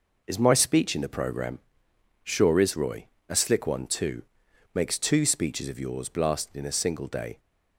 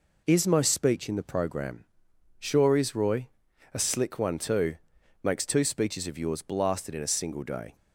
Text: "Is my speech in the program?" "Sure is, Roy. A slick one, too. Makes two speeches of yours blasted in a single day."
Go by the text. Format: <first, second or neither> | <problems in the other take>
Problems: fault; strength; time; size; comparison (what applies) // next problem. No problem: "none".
neither | none